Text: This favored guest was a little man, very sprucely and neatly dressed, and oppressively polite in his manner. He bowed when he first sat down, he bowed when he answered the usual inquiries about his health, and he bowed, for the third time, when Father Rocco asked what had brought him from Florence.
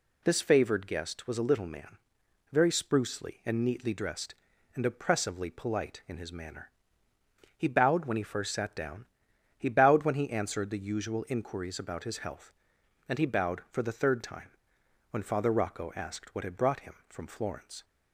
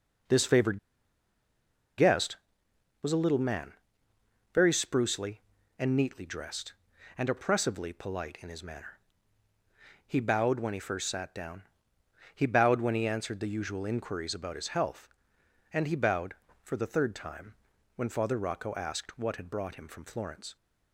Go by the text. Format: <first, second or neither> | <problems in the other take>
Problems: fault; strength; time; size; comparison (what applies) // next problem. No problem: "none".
first | pauses between "favored" and "guest"; at 0.7 s; 1.1 s long